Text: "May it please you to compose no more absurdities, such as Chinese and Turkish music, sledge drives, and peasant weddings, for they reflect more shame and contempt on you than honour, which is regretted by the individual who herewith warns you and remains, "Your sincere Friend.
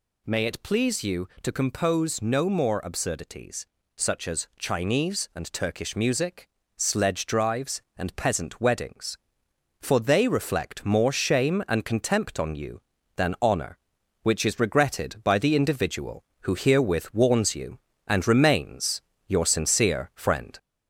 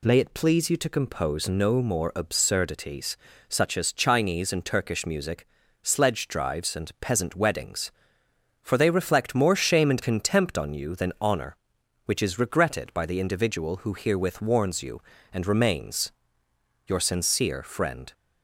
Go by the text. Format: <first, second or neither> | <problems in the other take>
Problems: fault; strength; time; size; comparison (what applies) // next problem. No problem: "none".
second | gets louder; slight; throughout; 2 dB